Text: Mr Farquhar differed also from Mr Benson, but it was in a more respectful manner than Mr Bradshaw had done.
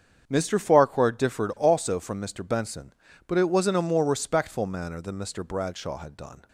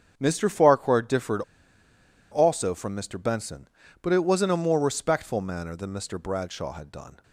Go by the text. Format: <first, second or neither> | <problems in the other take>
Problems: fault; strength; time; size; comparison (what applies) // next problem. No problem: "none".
first | starts louder than the rest; strong; until 1.1 s; 8 dB; strong in the first // pauses between "differed" and "also"; noticeable; at 1.4 s; 0.89 s long